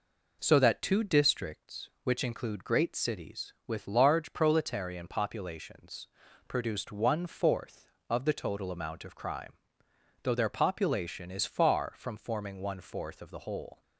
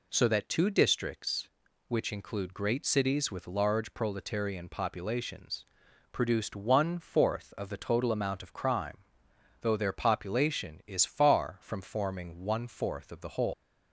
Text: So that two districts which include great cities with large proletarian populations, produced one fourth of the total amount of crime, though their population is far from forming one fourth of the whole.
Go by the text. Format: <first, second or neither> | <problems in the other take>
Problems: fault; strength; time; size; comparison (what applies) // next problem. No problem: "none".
first | leaves "whole" unfinished; at 13.5 s; 155 ms